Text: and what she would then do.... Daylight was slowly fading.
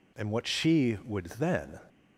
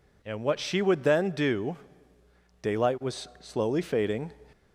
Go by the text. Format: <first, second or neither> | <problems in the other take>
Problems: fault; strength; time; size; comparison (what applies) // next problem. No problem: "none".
second | stops before "do Daylight was slowly fading"; at 1.8 s